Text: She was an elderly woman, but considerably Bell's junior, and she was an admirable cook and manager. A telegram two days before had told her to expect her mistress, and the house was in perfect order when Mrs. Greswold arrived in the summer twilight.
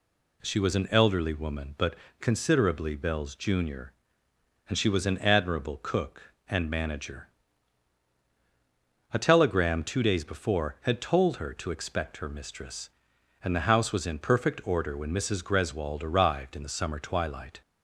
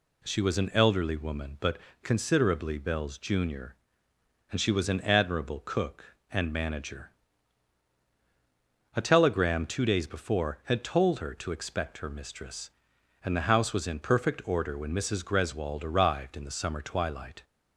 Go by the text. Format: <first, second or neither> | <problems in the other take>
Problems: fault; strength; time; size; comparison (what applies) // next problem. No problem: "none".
neither | pauses between "but" and "considerably"; slight; the same in both